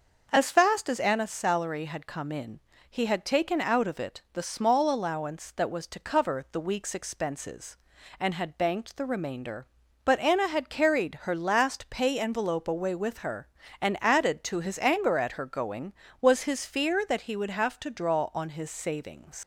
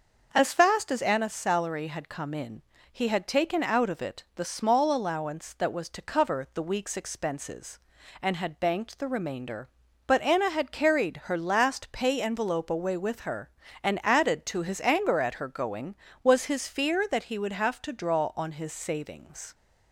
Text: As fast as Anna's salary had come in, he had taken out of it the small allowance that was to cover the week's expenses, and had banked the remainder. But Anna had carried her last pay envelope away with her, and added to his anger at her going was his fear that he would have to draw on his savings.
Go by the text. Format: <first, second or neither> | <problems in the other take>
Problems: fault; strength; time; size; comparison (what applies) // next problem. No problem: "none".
second | starts louder than the rest; until 1.3 s; 6.5 dB; also in the second // leaves "savings" unfinished; at 19.4 s; 90 ms